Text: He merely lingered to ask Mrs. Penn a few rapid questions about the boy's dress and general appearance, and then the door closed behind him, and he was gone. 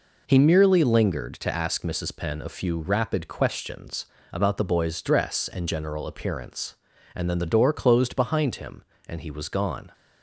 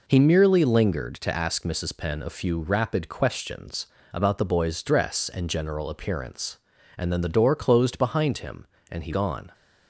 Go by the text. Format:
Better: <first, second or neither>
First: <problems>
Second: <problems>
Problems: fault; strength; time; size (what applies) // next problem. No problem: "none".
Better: first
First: pauses between "questions" and "about"; slight; at 4.0 s; 0.26 s long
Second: pauses between "questions" and "about"; slight; at 3.8 s; 0.26 s long // skips "was"; at 9.1 s